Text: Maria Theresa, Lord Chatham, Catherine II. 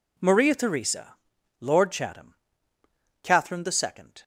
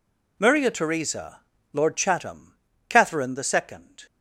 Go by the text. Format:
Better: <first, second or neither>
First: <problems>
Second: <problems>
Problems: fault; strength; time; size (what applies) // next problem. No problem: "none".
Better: neither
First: none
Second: none